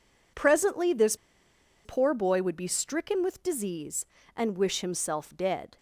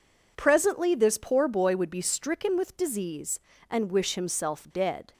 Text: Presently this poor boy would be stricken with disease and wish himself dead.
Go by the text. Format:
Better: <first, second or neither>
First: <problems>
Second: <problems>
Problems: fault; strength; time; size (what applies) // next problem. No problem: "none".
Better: second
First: pauses between "this" and "poor"; noticeable; at 1.1 s; 0.69 s long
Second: none